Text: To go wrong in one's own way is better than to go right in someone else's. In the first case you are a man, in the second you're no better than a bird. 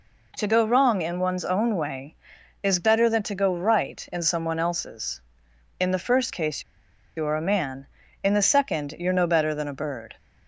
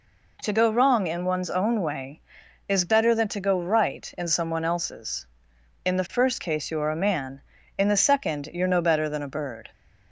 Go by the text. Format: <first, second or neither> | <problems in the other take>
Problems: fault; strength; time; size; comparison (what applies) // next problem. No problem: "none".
second | pauses between "case" and "you"; noticeable; at 6.6 s; 0.54 s long